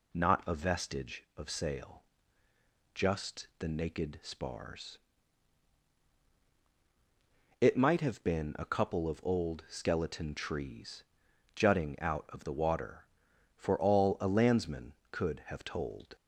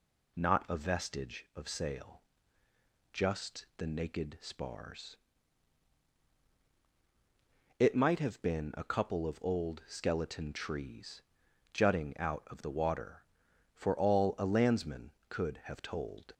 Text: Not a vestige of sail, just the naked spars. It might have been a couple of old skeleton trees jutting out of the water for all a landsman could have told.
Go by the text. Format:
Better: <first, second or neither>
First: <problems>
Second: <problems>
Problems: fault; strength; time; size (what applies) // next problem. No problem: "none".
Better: neither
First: pauses between "trees" and "jutting"; noticeable; at 11.0 s; 0.52 s long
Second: pauses between "trees" and "jutting"; noticeable; at 11.2 s; 0.51 s long